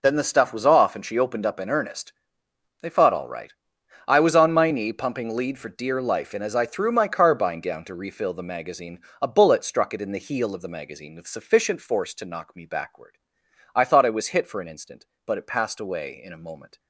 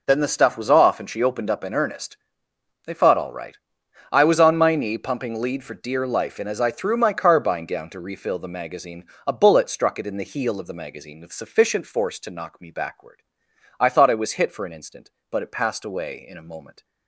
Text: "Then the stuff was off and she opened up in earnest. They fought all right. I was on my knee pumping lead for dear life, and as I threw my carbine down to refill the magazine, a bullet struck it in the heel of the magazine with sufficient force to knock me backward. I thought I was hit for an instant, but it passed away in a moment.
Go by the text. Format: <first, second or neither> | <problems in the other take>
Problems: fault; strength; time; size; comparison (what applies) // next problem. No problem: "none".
neither | none